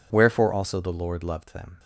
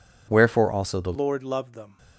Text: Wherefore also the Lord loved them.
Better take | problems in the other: first | changes voice at "Lord"; from 1.1 s on; 0.8 s long

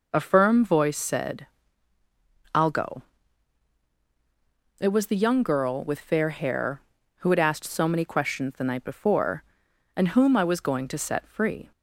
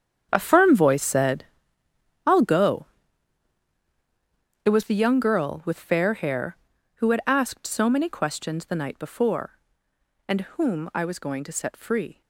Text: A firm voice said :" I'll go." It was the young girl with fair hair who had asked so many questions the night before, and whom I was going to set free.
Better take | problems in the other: first | gets quieter; throughout; 6.5 dB

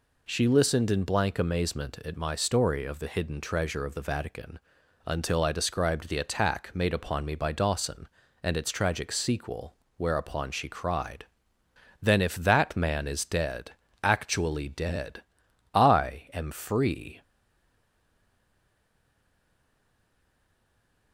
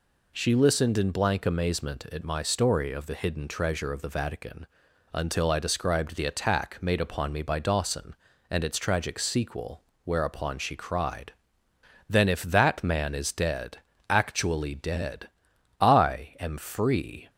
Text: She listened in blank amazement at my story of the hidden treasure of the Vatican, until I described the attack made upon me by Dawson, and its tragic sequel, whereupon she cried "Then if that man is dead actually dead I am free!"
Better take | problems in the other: second | pauses between "cried" and "Then"; noticeable; at 11.2 s; 0.78 s long; noticeable in the second // pauses between "dead" and "actually"; slight; at 13.7 s; 0.32 s long; slight in the second // pauses between "dead" and "I"; noticeable; at 15.2 s; 0.52 s long; noticeable in the second // stays silent after the last word; strong; from 17.2 s on; 3.9 s long

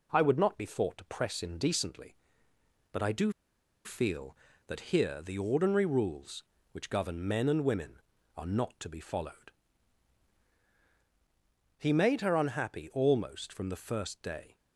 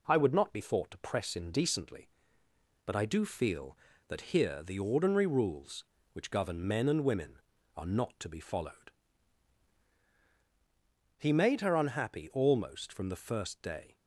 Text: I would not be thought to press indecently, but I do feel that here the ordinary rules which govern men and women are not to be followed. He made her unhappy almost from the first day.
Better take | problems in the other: second | pauses between "do" and "feel"; noticeable; at 3.3 s; 0.54 s long

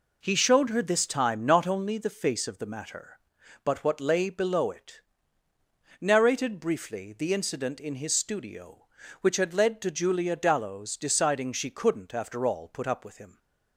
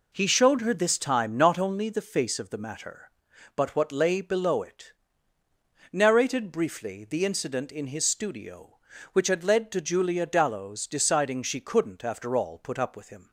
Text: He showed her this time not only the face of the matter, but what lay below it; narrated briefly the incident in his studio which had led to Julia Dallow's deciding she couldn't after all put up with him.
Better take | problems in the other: neither | none

